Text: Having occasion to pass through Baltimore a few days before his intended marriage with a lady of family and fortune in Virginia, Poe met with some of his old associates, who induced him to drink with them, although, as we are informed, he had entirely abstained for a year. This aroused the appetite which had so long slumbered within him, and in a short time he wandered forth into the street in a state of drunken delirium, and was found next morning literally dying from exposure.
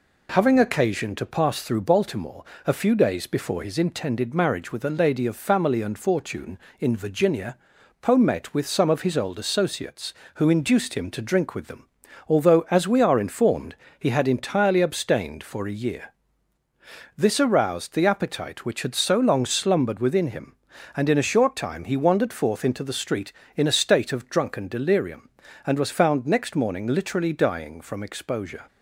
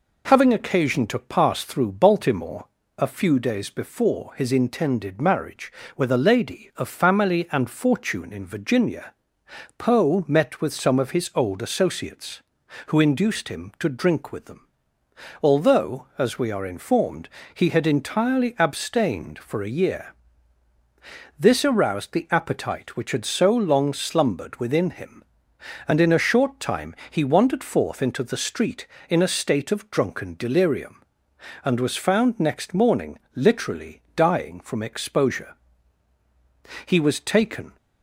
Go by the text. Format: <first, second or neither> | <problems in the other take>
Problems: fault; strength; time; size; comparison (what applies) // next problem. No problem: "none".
first | pauses between "Baltimore" and "a"; slight; at 2.6 s; 0.32 s long; slight in the first // pauses between "time" and "he"; slight; at 26.9 s; 0.16 s long // pauses between "morning" and "literally"; slight; at 33.1 s; 0.16 s long // goes on to say "He was taken"; noticeable; from 36.8 s on; 0.92 s long